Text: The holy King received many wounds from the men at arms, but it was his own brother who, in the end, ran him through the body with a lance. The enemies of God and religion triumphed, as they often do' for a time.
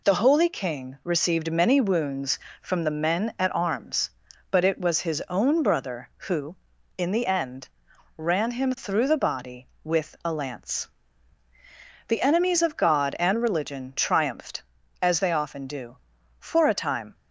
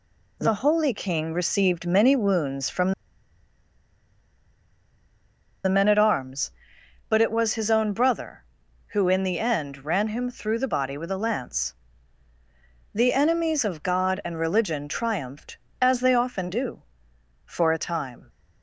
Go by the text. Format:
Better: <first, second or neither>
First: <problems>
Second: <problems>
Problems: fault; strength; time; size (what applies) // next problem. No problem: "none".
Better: first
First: none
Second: pauses between "from" and "the"; strong; at 2.9 s; 2.7 s long